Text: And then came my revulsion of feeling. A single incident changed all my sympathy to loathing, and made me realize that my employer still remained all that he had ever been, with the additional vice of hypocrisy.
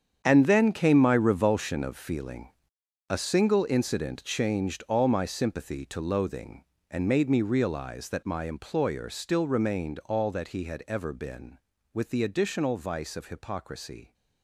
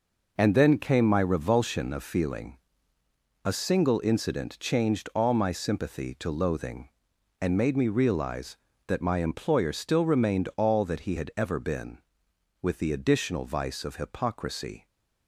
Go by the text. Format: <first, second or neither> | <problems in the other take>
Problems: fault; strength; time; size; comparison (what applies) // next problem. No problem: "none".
second | gets quieter; strong; throughout; 13 dB